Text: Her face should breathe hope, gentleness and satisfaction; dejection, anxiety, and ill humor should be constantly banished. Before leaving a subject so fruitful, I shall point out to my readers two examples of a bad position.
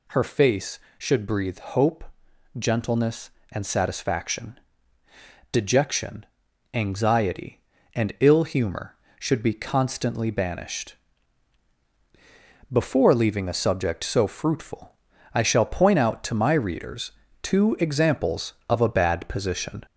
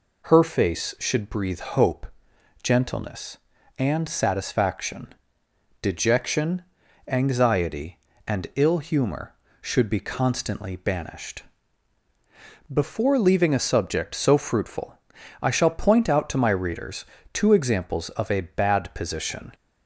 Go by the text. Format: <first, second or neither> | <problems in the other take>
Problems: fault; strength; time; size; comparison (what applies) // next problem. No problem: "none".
second | gets louder; throughout; 3.5 dB // pauses between "readers" and "two"; slight; at 17.1 s; 0.32 s long; slight in the second